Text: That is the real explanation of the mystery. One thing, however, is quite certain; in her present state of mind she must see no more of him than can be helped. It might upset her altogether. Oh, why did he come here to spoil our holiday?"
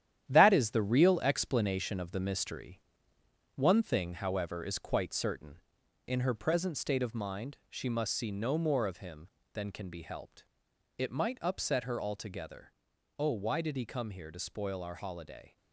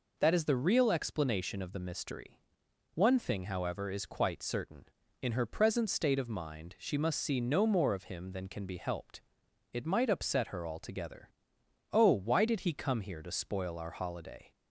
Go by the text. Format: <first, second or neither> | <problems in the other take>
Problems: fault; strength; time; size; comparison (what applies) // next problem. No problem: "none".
second | gets quieter; strong; throughout; 8 dB